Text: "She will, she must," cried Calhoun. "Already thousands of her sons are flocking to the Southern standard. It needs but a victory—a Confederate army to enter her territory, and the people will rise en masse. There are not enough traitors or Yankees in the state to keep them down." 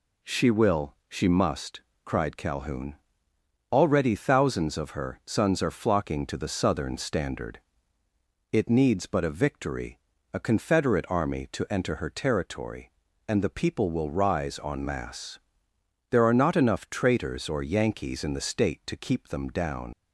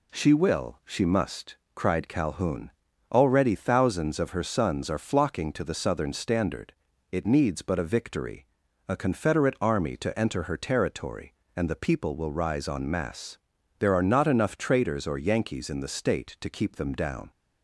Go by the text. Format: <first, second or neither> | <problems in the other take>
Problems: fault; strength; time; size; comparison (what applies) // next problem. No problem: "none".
second | leaves "down" unfinished; at 19.9 s; 80 ms